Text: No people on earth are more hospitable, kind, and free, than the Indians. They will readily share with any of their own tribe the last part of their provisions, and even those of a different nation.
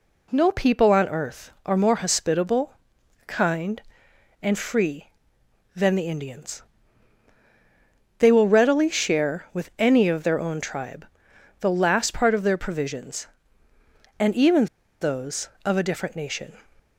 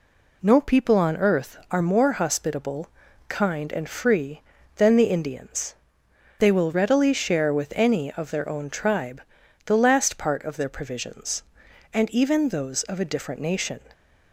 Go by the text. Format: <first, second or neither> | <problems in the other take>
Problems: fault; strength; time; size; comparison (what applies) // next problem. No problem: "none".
second | pauses between "tribe" and "the"; noticeable; at 11.0 s; 0.54 s long; noticeable in the second // pauses between "even" and "those"; slight; at 14.6 s; 0.35 s long